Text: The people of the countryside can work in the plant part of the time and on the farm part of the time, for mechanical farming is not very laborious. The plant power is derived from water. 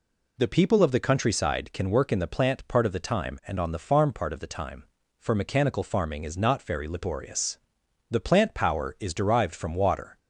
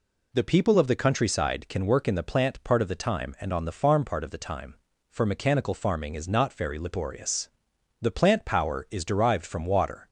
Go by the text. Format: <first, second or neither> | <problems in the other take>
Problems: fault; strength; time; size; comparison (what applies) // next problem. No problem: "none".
neither | none